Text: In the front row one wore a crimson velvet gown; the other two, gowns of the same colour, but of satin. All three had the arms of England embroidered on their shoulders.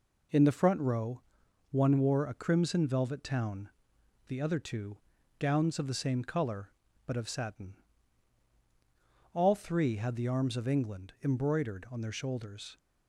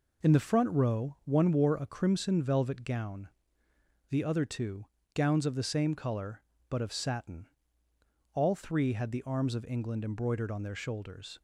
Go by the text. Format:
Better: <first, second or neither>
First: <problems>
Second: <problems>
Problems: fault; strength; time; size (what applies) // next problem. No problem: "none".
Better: second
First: pauses between "row" and "one"; noticeable; at 1.2 s; 0.50 s long // says "town" for "gown"; at 3.2 s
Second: none